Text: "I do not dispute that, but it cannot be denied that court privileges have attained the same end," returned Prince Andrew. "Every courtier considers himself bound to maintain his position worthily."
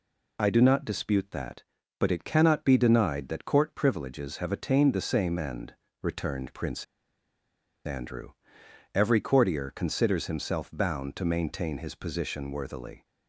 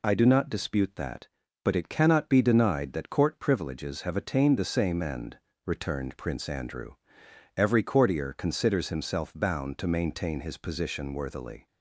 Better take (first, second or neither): second